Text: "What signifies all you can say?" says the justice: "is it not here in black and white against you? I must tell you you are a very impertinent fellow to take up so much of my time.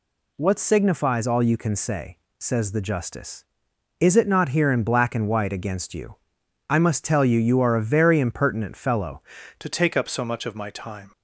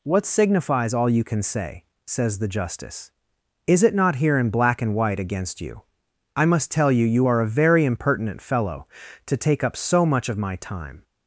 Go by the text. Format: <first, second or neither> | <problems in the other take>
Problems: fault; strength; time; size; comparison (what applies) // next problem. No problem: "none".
second | changes voice at "to"; from 9.5 s on; 1.6 s long